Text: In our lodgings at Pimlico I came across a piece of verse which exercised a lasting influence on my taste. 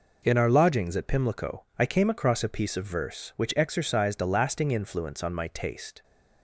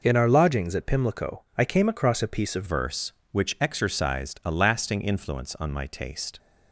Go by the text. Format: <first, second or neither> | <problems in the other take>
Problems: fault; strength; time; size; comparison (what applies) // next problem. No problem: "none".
first | changes voice at "verse"; from 2.6 s on; 3.7 s long